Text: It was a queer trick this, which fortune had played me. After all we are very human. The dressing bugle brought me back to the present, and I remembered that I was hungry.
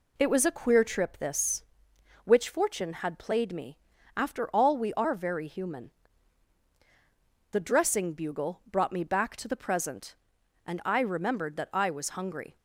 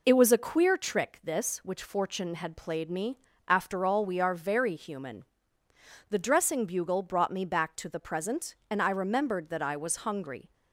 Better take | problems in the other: second | says "trip" for "trick"; at 0.8 s

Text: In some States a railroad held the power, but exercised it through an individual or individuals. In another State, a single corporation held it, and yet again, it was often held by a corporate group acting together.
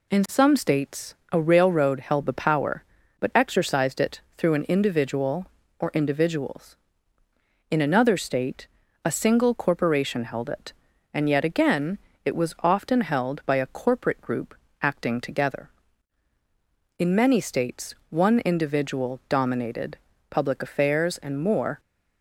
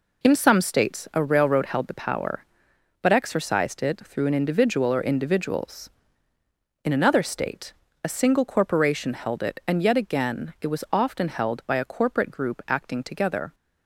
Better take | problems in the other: second | pauses between "States" and "a"; slight; at 1.1 s; 0.16 s long // pauses between "it" and "through"; slight; at 4.2 s; 0.16 s long // pauses between "group" and "acting"; slight; at 14.5 s; 0.28 s long // goes on to say "In many States one individual dominated public affairs and more"; strong; from 16.9 s on; 4.8 s long

